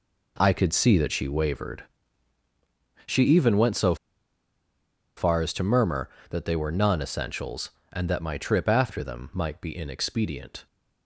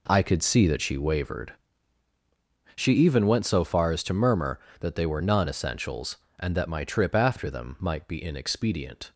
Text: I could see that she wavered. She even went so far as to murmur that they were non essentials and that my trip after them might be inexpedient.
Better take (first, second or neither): second